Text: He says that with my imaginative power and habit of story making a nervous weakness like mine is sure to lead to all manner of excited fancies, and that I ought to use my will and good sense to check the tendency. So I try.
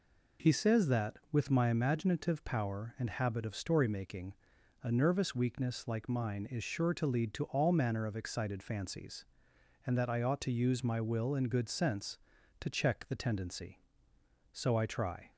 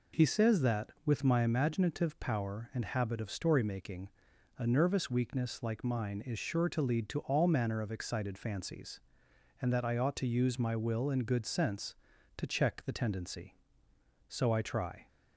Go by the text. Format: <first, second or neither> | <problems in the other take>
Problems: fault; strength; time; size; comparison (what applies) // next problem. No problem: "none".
neither | pauses between "making" and "a"; noticeable; the same in both